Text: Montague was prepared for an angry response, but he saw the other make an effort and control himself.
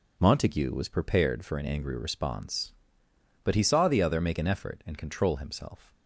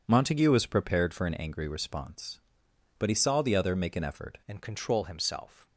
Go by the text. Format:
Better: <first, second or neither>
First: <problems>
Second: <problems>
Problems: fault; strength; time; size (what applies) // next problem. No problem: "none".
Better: first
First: none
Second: changes voice at "and"; from 4.4 s on; 1.2 s long